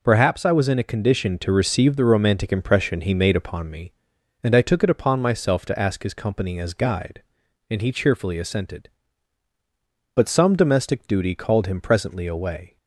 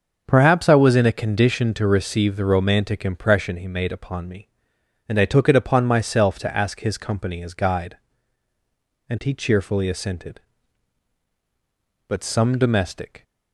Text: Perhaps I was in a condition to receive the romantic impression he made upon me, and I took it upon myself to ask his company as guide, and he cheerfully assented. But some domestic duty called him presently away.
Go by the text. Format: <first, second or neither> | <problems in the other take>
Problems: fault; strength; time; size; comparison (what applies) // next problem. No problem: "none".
first | starts louder than the rest; until 1.2 s; 6.5 dB // stops before "duty called him presently away"; at 13.2 s